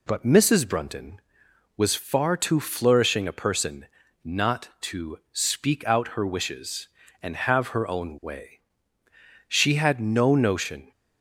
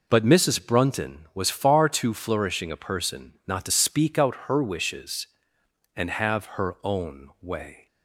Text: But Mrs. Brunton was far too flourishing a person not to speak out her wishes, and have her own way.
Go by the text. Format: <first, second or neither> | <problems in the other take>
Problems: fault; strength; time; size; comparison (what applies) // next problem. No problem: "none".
second | pauses between "person" and "not"; at 3.8 s; 0.38 s long // goes on to say "She had no notion"; from 9.4 s on; 1.4 s long